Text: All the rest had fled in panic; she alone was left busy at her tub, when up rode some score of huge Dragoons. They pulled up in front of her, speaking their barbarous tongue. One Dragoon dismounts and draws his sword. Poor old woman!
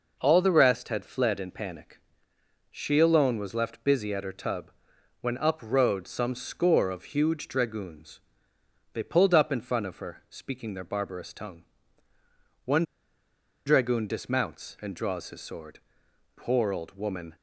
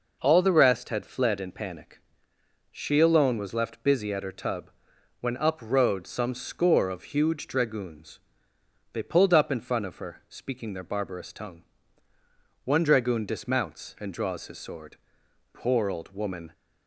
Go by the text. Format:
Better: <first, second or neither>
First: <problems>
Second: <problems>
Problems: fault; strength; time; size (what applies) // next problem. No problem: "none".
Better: second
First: pauses between "One" and "Dragoon"; noticeable; at 12.8 s; 0.83 s long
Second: none